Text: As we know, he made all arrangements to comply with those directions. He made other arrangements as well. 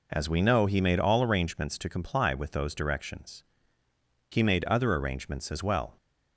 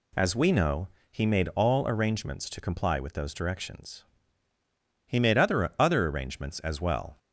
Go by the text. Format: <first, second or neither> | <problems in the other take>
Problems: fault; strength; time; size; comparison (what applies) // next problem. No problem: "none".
first | says "other" twice; at 5.7 s